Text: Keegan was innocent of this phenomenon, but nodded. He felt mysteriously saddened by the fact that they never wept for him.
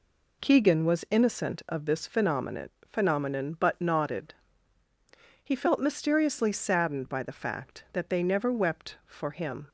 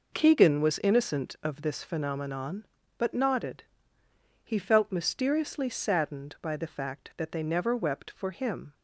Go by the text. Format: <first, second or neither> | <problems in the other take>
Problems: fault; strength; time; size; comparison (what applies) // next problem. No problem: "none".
second | says "phenomenon" twice; at 2.9 s